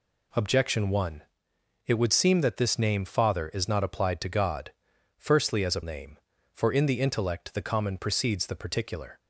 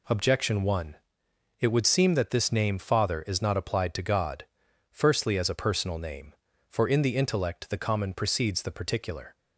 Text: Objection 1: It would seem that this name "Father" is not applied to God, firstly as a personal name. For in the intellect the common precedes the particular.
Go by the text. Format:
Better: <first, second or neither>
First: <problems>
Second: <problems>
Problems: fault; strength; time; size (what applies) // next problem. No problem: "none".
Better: second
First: skips "personal"; at 5.8 s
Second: none